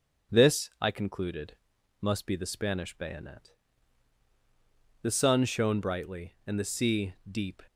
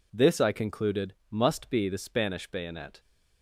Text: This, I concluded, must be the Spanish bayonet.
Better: second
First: starts louder than the rest; until 1.4 s; 7 dB // goes on to say "The sun shone brightly and the sea deep"; strong; from 5.0 s on; 2.6 s long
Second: none

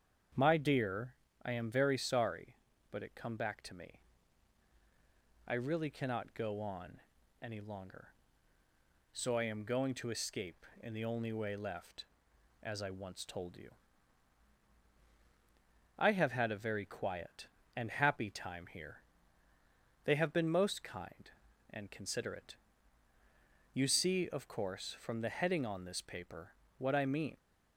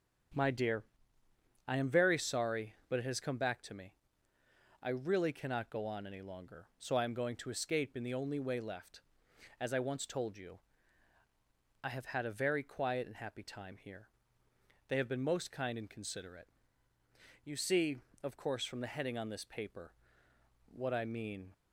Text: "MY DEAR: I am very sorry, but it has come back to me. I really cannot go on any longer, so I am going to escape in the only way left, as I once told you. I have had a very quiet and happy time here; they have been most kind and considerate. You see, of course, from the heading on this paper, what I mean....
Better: second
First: starts louder than the rest; strong; until 1.6 s; 7.5 dB // skips "has"; at 3.1 s // pauses between "on" and "any"; at 7.0 s; 0.38 s long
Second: starts louder than the rest; strong; until 2.1 s; 7.5 dB

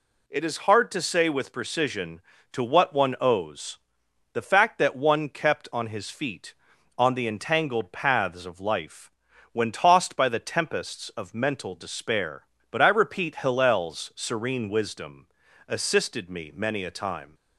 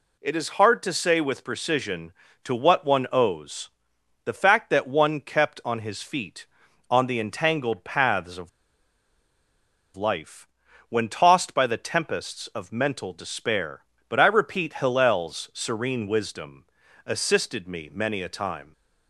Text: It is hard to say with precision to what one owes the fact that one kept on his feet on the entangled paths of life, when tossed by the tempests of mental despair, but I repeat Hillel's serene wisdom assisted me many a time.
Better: first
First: pauses between "owes" and "the"; noticeable; at 3.7 s; 0.54 s long // pauses between "wisdom" and "assisted"; at 15.2 s; 0.40 s long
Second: pauses between "owes" and "the"; noticeable; at 3.6 s; 0.54 s long // pauses between "of" and "life"; strong; at 8.4 s; 1.4 s long // pauses between "wisdom" and "assisted"; at 16.6 s; 0.40 s long

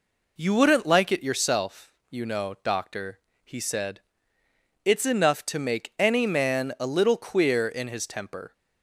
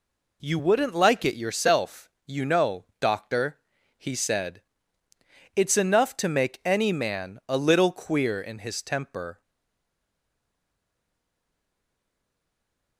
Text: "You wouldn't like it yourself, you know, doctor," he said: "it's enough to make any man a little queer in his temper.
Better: first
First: none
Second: stays silent after the last word; strong; from 9.4 s on; 3.5 s long

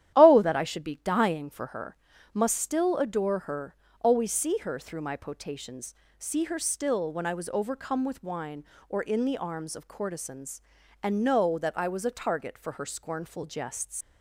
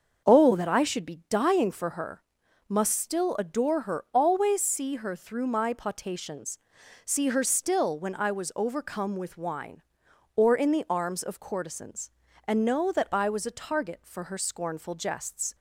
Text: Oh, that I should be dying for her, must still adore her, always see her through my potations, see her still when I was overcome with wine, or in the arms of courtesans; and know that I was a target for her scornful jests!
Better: second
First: starts louder than the rest; strong; until 1.1 s; 11.5 dB // leaves "jests" unfinished; at 14.0 s; 115 ms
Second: starts louder than the rest; until 1.3 s; 6.5 dB

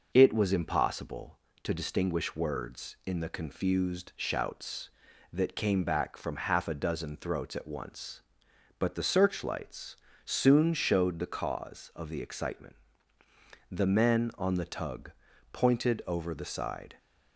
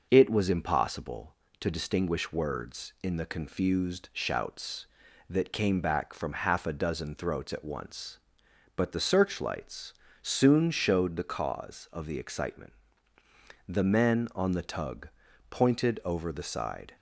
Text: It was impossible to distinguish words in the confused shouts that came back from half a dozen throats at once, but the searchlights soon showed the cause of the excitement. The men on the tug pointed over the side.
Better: neither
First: pauses between "searchlights" and "soon"; slight; at 9.9 s; 0.30 s long // pauses between "tug" and "pointed"; at 15.1 s; 0.41 s long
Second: pauses between "searchlights" and "soon"; slight; at 9.9 s; 0.30 s long // pauses between "tug" and "pointed"; at 15.0 s; 0.40 s long

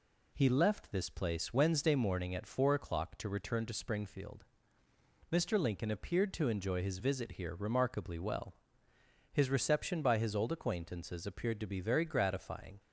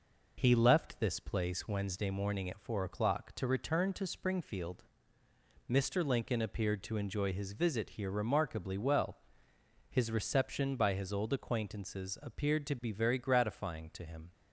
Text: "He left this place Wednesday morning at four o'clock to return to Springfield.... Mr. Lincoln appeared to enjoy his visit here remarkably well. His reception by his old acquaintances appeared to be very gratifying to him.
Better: second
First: stops before "to him"; at 12.7 s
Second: none

